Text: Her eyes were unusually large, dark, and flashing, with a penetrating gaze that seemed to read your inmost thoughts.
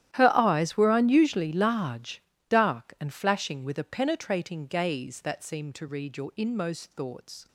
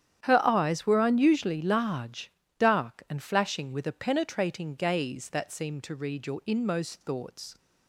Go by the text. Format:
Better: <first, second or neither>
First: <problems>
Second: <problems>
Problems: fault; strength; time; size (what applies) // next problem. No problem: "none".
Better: second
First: gets quieter; strong; throughout; 18 dB // starts louder than the rest; strong; until 1.2 s; 12 dB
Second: starts louder than the rest; strong; until 1.3 s; 10 dB